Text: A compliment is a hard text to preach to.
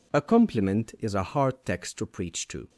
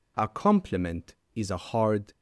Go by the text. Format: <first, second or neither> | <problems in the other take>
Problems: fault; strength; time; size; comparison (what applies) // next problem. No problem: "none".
first | stops before "text to preach to"; at 2.1 s